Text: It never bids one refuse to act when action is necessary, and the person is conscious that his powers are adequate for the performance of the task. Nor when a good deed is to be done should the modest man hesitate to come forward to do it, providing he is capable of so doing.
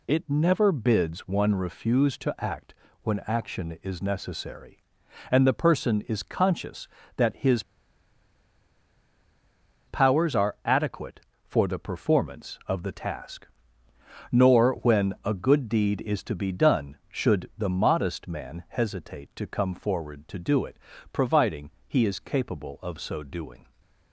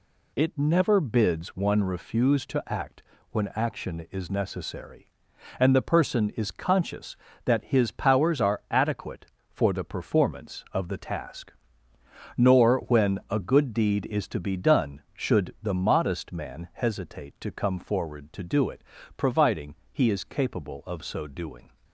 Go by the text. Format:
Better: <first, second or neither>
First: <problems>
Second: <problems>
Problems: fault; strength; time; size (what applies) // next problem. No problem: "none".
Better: second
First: pauses between "act" and "when"; slight; at 2.7 s; 0.28 s long // pauses between "his" and "powers"; strong; at 7.6 s; 2.2 s long // pauses between "providing" and "he"; slight; at 21.6 s; 0.16 s long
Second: pauses between "act" and "when"; slight; at 3.0 s; 0.28 s long // pauses between "providing" and "he"; slight; at 19.7 s; 0.16 s long